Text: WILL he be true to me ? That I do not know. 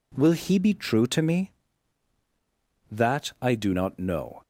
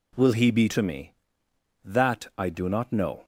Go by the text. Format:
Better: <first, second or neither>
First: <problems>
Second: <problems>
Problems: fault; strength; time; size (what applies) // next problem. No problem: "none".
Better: first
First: none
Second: skips "true"; at 0.6 s